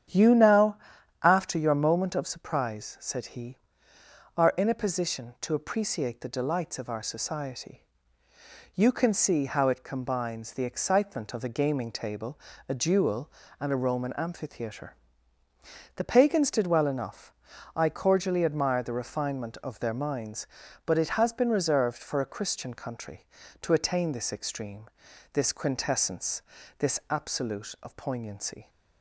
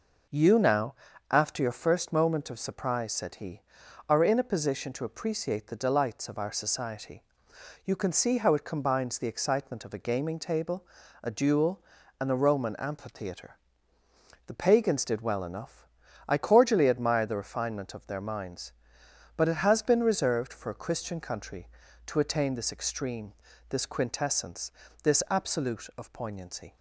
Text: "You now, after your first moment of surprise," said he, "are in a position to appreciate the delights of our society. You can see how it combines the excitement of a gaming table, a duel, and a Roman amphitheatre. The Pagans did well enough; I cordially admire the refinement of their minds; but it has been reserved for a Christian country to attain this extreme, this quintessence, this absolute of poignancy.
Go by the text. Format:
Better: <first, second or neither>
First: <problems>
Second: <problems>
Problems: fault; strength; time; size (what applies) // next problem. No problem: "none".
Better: second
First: starts louder than the rest; strong; until 1.5 s; 9 dB // skips "first"; at 1.7 s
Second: none